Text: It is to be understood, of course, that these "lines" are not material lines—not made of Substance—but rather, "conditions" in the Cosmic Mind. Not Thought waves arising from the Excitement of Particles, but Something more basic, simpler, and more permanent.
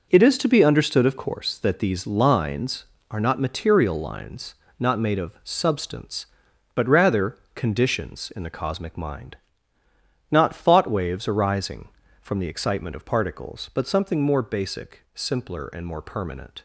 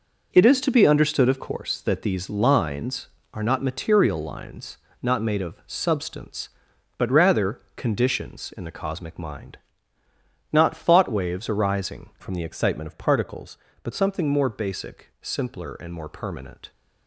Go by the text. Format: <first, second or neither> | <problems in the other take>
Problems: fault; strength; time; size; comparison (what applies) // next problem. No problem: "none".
first | changes voice from "from" to "but"; from 12.1 to 13.9 s; 1.8 s long